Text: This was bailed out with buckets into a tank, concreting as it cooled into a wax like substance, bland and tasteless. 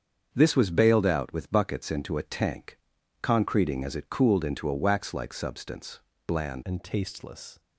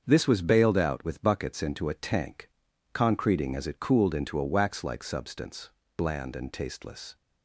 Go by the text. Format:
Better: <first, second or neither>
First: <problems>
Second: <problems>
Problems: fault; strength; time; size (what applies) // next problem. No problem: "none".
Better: second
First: starts louder than the rest; strong; until 1.3 s; 7 dB // changes voice at "and"; from 6.6 s on; 0.9 s long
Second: starts louder than the rest; until 1.0 s; 7 dB